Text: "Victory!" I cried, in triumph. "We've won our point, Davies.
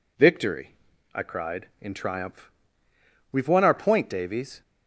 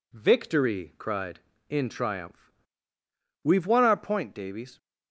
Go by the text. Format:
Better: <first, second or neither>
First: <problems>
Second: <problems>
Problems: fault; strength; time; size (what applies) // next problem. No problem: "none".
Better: first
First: none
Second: skips "I"; at 0.9 s